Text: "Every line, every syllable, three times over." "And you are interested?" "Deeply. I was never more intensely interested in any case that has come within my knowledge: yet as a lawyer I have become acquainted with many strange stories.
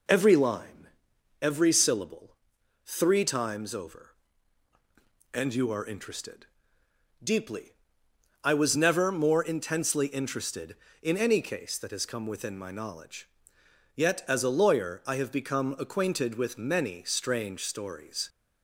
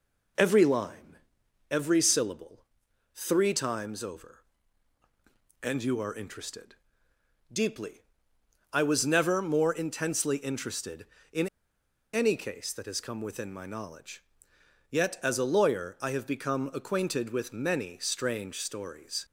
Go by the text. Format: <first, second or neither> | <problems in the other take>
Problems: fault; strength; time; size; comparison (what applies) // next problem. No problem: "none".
first | pauses between "in" and "any"; noticeable; at 11.4 s; 0.66 s long